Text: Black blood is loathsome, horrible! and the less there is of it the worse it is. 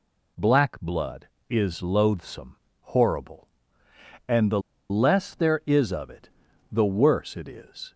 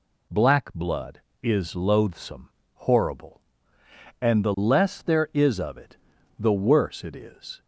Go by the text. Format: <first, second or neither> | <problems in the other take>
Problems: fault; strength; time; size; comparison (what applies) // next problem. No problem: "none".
second | pauses between "the" and "less"; slight; at 4.5 s; 0.30 s long // pauses between "it" and "the"; at 6.2 s; 0.42 s long; also in the second